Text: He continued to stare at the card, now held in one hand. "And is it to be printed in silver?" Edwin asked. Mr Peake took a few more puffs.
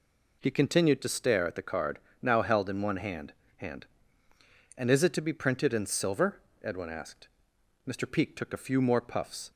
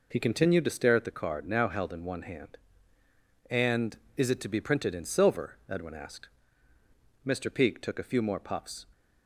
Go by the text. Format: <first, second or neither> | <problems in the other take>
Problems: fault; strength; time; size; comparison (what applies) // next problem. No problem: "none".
second | says "hand" twice; at 3.5 s